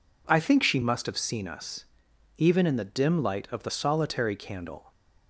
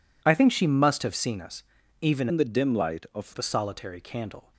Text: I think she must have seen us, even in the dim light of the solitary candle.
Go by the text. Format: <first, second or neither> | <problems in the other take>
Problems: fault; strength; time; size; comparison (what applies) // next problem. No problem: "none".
first | changes voice from "in" to "of"; from 2.2 to 3.3 s; 1.1 s long